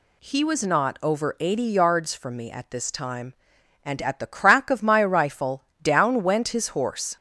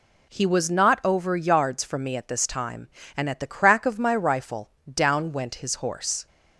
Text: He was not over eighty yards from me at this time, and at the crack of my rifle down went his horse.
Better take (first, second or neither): first